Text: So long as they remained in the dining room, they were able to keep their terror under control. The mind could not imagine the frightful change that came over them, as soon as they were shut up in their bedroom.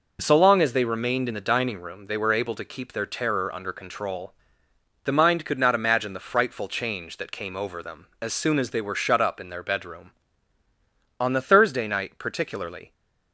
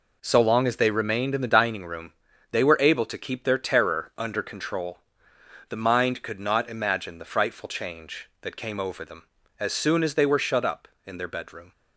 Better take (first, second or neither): second